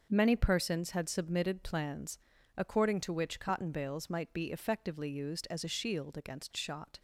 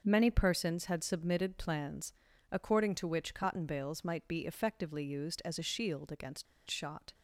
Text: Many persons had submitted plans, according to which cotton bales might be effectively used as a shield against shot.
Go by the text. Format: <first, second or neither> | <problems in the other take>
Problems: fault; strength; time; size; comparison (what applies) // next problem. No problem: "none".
first | pauses between "against" and "shot"; slight; at 6.4 s; 0.24 s long